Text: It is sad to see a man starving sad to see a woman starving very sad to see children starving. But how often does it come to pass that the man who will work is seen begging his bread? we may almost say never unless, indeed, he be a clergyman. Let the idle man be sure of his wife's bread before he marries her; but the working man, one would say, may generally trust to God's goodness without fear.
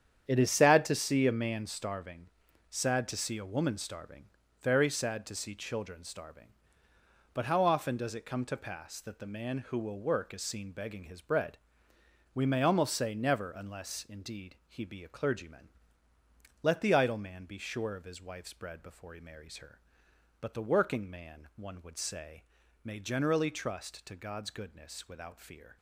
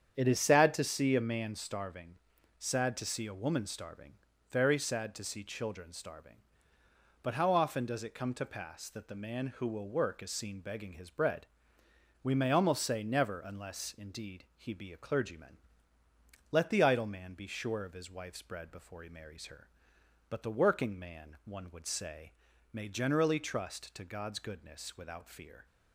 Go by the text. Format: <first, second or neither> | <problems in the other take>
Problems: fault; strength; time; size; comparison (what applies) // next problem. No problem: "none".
second | gets quieter; strong; throughout; 10.5 dB // starts louder than the rest; strong; until 1.2 s; 8.5 dB; strong in the second // pauses between "starving" and "sad"; at 2.2 s; 0.42 s long; also in the second // pauses between "starving" and "very"; slight; at 4.2 s; 0.36 s long; slight in the second